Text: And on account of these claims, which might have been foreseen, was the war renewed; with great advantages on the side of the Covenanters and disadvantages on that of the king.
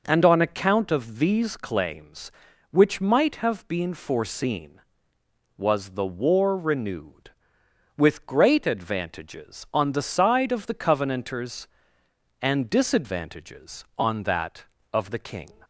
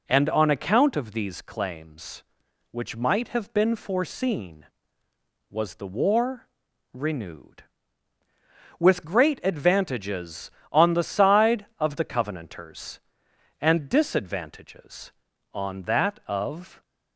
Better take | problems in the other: first | pauses between "war" and "renewed"; at 6.4 s; 0.44 s long // stops before "the king"; at 16.8 s

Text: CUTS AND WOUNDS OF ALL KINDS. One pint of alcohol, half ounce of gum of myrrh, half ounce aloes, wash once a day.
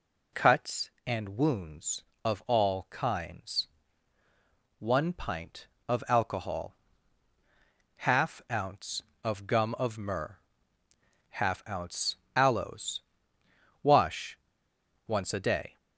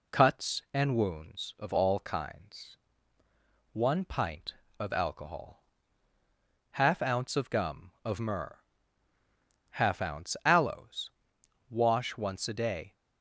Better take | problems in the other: second | pauses between "ounce" and "aloes"; slight; at 12.1 s; 0.18 s long // pauses between "wash" and "once"; noticeable; at 14.3 s; 0.70 s long

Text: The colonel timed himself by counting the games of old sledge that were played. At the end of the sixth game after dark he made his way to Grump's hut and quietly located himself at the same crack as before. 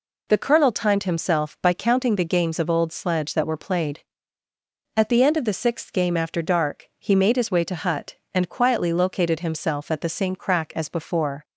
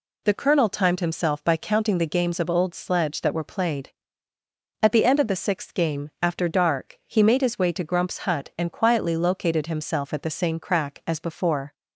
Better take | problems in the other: second | skips "Grump's"; at 7.7 s

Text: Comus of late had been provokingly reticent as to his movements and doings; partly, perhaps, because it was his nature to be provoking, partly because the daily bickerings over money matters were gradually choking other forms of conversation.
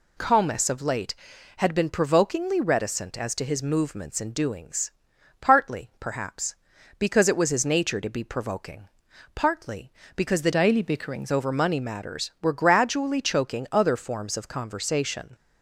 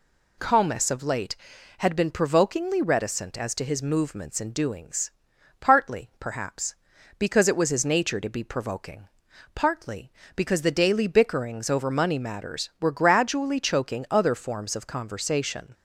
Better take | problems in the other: second | changes voice from "daily" to "bickerings"; from 10.5 to 11.3 s; 0.8 s long

